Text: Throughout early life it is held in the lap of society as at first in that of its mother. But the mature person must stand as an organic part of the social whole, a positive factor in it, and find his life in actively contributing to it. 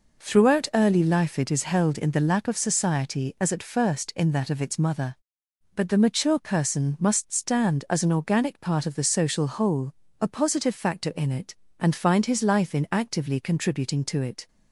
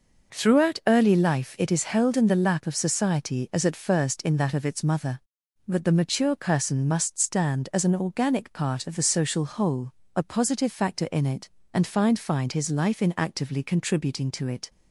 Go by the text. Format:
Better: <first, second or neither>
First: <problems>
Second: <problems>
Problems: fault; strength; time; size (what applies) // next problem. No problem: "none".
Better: first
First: none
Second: says "find" twice; at 12.1 s